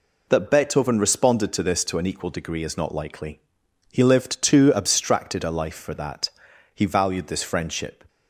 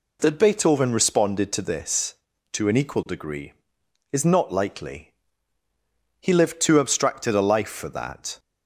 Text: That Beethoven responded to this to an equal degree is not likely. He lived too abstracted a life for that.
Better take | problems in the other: second | goes on to say "He valued this friendship"; from 6.7 s on; 1.3 s long

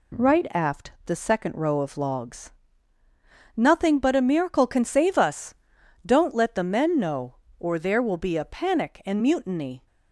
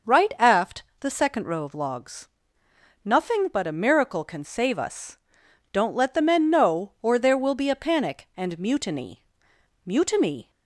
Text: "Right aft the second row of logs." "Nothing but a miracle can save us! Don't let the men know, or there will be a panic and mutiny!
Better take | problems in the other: first | pauses between "aft" and "the"; slight; at 0.8 s; 0.16 s long; slight in the first // says "mutiny" twice; at 9.8 s

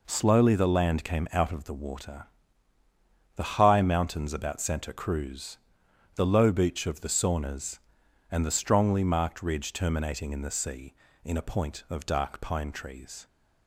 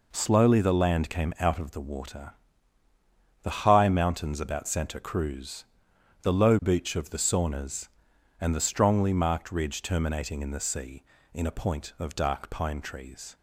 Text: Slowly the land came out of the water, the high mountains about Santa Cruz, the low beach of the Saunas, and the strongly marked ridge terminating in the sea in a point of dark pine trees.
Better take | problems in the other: neither | none

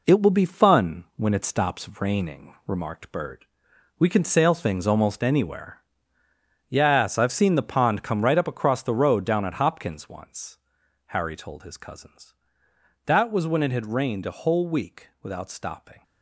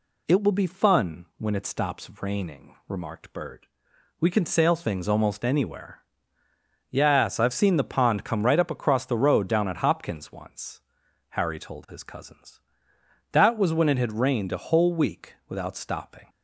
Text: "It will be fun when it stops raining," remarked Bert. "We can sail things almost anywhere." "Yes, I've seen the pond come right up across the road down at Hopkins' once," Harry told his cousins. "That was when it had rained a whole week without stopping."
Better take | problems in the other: second | gets quieter; strong; throughout; 7 dB

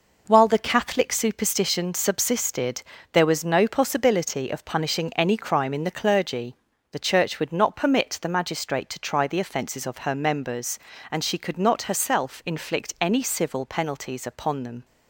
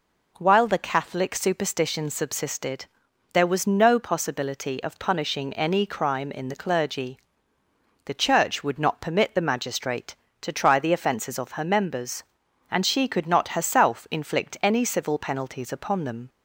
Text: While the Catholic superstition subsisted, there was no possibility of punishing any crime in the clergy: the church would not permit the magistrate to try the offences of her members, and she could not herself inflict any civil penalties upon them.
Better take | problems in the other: neither | none

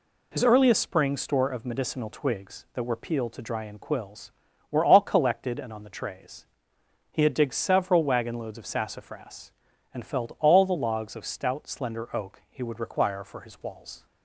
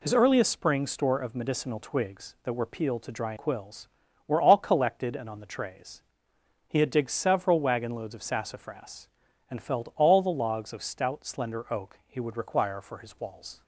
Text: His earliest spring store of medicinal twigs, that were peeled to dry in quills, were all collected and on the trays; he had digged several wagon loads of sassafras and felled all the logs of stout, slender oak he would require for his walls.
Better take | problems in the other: first | skips "in"; at 3.3 s

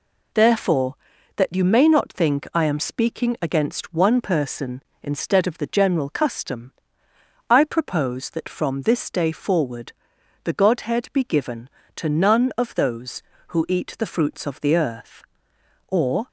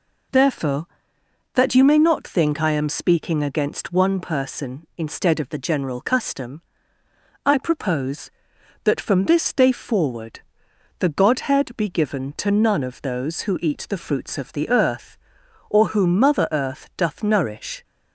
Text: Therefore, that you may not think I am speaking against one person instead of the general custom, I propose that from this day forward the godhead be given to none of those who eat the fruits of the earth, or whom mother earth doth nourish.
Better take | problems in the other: second | pauses between "forward" and "the"; noticeable; at 9.9 s; 0.52 s long; noticeable in the second // stops before "whom mother earth doth nourish"; at 16.2 s

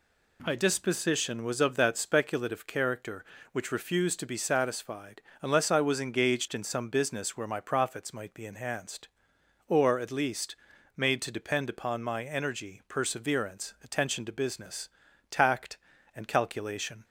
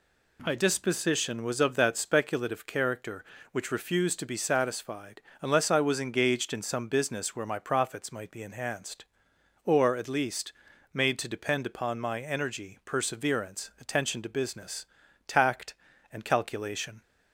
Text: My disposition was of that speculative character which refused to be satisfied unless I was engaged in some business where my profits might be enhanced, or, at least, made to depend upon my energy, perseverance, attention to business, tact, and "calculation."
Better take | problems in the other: neither | pauses between "satisfied" and "unless"; slight; the same in both

